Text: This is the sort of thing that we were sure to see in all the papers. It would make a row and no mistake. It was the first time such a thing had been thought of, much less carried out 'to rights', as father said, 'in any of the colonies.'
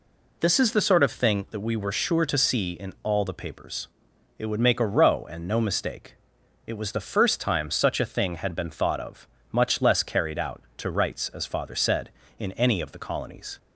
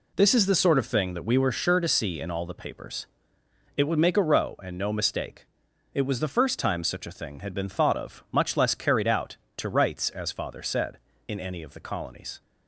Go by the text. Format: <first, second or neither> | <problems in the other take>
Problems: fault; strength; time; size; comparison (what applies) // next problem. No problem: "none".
neither | none